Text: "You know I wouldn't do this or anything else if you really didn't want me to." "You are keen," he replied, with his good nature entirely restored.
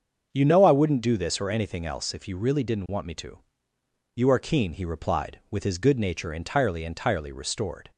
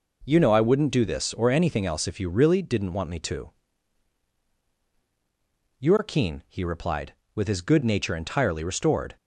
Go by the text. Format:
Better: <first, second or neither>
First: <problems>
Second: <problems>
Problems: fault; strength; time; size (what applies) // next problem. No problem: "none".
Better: second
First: starts louder than the rest; until 1.3 s; 7 dB // says "entirely" twice; at 6.8 s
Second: none